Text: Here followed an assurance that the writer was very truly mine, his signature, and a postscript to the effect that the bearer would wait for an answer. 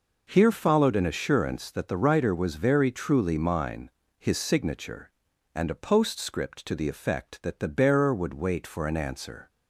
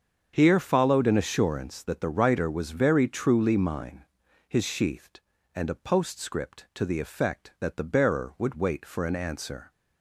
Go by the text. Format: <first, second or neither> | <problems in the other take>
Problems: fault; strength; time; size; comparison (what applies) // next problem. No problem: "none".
first | starts louder than the rest; strong; until 1.3 s; 7 dB // says "sheathed" for "signature"; at 4.6 s